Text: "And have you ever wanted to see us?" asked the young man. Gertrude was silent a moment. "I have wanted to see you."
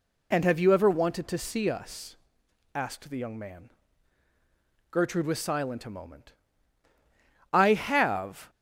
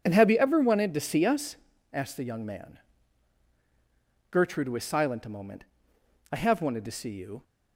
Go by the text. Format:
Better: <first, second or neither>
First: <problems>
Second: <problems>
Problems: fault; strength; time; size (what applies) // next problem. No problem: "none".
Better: second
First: stops before "wanted to see you"; at 8.4 s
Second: none